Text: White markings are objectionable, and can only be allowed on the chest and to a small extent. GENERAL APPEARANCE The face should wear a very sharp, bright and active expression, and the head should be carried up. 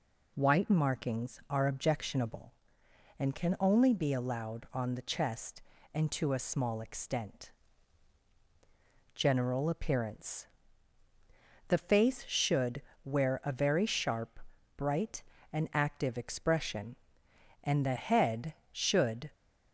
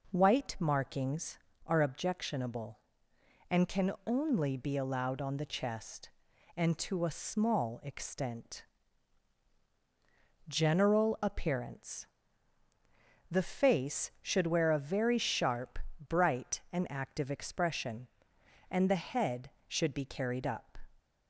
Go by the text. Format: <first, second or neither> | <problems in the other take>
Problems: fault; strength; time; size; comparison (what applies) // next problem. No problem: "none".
second | pauses between "APPEARANCE" and "The"; at 10.4 s; 1.2 s long; also in the second // pauses between "should" and "wear"; slight; at 12.8 s; 0.24 s long // stops before "be carried up"; at 19.3 s